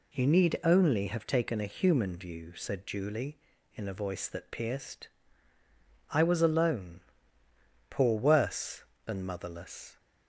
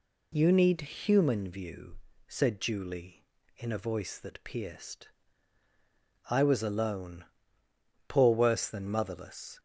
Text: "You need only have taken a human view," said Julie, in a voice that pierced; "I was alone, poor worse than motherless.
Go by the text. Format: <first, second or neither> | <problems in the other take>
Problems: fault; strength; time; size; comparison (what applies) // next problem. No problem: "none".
first | skips "only have taken a"; at 0.8 s